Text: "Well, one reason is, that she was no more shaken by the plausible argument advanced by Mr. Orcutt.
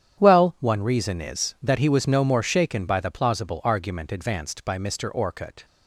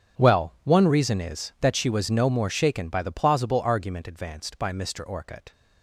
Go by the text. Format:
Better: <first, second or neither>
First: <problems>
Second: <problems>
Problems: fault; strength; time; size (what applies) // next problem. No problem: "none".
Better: second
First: starts louder than the rest; strong; until 1.2 s; 9.5 dB // says "he" for "she"; at 1.7 s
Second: starts louder than the rest; strong; until 1.2 s; 8.5 dB